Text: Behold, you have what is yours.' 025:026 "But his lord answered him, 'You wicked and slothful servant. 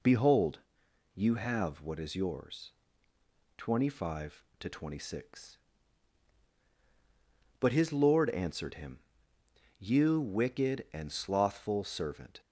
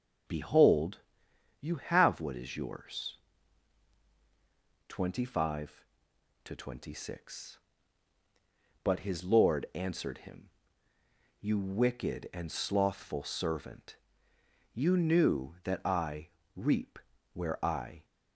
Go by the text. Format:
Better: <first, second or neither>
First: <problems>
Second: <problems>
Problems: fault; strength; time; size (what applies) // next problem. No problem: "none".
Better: first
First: none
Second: goes on to say "You knew that I reap where I"; strong; from 14.7 s on; 3.3 s long